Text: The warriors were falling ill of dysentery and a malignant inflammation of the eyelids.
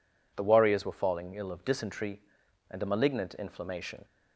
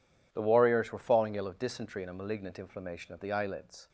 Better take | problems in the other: second | stops before "of the eyelids"; at 4.0 s

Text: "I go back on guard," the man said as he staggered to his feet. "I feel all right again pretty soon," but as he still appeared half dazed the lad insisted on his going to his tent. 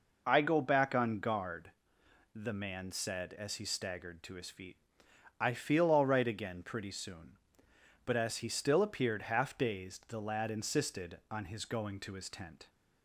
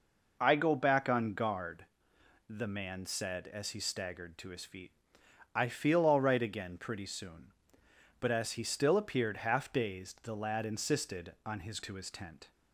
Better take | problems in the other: first | skips "going"; at 11.8 s

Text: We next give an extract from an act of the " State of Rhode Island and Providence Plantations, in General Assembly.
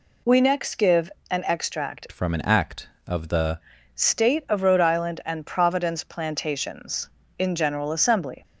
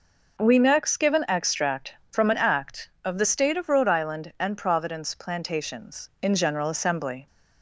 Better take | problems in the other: second | pauses between "give" and "an"; slight; at 1.0 s; 0.20 s long // changes voice from "from" to "the"; from 2.1 to 3.5 s; 1.4 s long

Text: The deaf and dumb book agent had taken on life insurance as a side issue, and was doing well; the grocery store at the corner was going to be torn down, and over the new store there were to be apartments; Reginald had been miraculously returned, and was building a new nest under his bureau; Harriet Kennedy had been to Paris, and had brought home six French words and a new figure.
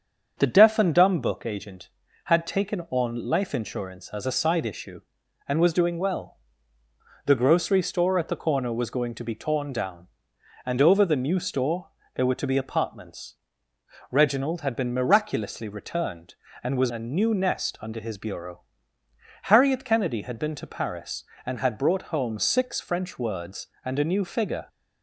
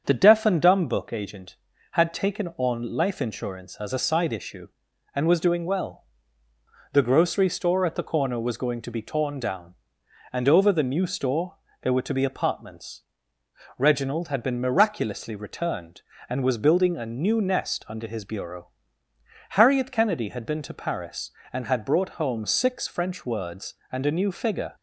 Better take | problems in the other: second | starts louder than the rest; strong; until 1.3 s; 7 dB; strong in the second // pauses between "store" and "there"; slight; at 11.8 s; 0.26 s long; slight in the second // skips "building"; at 16.9 s

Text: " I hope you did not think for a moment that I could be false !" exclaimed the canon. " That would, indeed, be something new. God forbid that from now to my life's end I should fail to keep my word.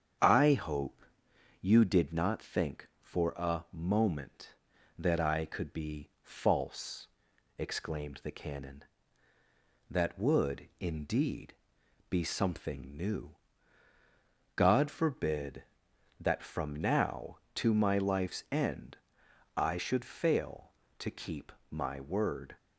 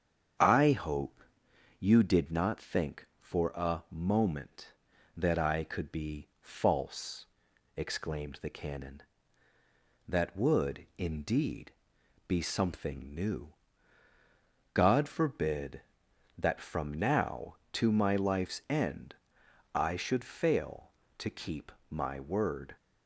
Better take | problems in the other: neither | starts louder than the rest; strong; the same in both // pauses between "hope" and "you"; noticeable; the same in both // pauses between "end" and "I"; noticeable; the same in both // pauses between "keep" and "my"; slight; the same in both

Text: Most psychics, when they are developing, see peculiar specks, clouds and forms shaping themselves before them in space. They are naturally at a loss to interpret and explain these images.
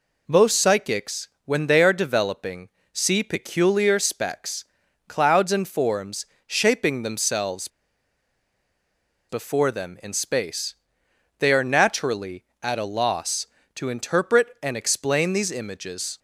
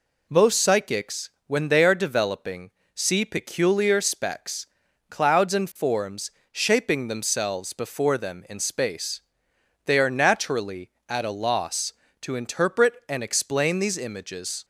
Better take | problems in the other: second | pauses between "forms" and "shaping"; slight; at 6.2 s; 0.22 s long; slight in the second // pauses between "themselves" and "before"; strong; at 7.6 s; 1.6 s long

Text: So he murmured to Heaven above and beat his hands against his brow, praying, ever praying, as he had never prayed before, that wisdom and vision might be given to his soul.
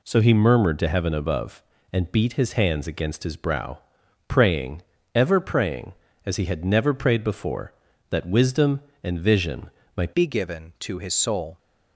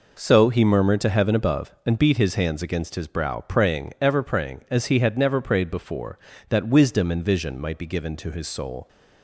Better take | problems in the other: second | pauses between "vision" and "might"; slight; at 9.6 s; 0.26 s long // changes voice at "be"; from 10.1 s on; 1.4 s long

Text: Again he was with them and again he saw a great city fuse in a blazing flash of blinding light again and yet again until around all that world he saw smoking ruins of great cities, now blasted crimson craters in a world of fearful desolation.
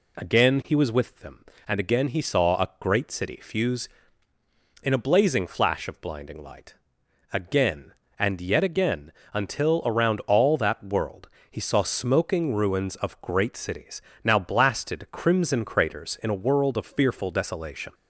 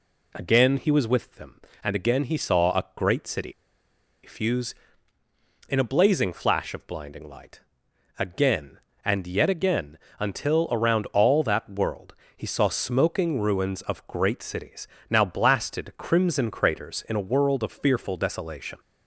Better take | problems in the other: first | pauses between "city" and "fuse"; noticeable; at 3.5 s; 0.74 s long // pauses between "light" and "again"; noticeable; at 7.6 s; 0.56 s long; noticeable in the first // pauses between "again" and "until"; slight; at 9.9 s; 0.20 s long; slight in the first // pauses between "world" and "he"; slight; at 12.1 s; 0.22 s long; slight in the first

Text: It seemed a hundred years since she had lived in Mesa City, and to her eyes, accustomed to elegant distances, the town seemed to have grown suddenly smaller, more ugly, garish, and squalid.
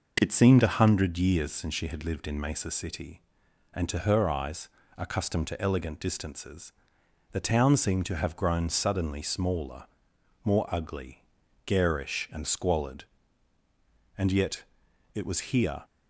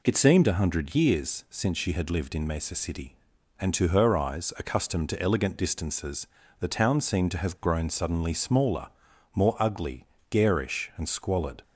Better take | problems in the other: second | goes on to say "And yet it was here"; from 14.1 s on; 1.6 s long

